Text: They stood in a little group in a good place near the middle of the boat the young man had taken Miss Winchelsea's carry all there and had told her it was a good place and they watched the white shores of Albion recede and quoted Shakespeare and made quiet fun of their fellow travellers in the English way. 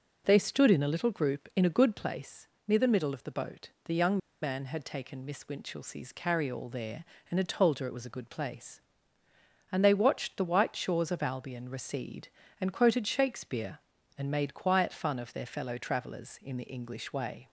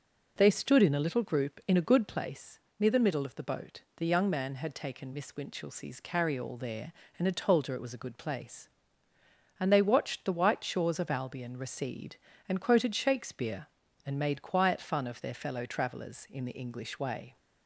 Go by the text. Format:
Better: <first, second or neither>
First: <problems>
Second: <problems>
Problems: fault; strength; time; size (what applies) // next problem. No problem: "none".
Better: second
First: pauses between "place" and "near"; slight; at 2.4 s; 0.20 s long // pauses between "boat" and "the"; slight; at 3.6 s; 0.16 s long // pauses between "young" and "man"; slight; at 4.1 s; 0.24 s long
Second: pauses between "place" and "near"; slight; at 2.5 s; 0.20 s long // pauses between "boat" and "the"; slight; at 3.8 s; 0.16 s long